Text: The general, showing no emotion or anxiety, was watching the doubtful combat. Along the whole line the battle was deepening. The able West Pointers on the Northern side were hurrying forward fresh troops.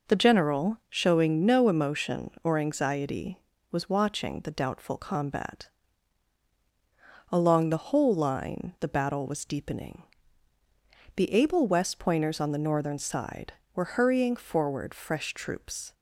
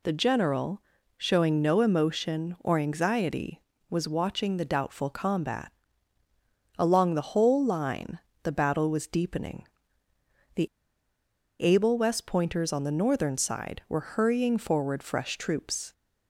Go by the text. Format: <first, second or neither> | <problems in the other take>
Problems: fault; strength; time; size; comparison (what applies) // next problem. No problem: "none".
first | pauses between "line" and "the"; slight; at 8.1 s; 0.26 s long // pauses between "The" and "able"; noticeable; at 10.6 s; 0.94 s long